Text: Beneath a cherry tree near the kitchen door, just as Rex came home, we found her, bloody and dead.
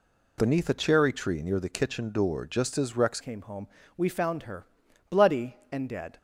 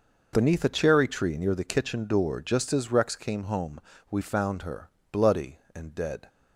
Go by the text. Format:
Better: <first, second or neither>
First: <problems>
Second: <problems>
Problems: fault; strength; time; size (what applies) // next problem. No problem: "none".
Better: second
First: changes voice at "came"; from 3.2 s on; 2.9 s long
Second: none